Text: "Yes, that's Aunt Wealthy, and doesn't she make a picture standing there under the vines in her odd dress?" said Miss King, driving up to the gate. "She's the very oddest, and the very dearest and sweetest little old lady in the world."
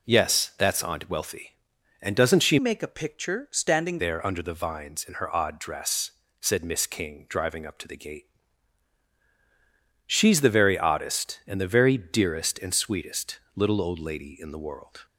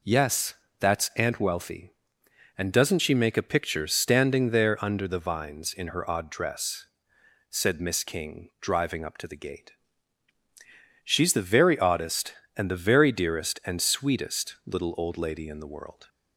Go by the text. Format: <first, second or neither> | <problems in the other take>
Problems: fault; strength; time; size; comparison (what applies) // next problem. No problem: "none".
second | changes voice from "make" to "standing"; from 2.5 to 3.9 s; 1.4 s long // pauses between "sweetest" and "little"; slight; at 13.3 s; 0.18 s long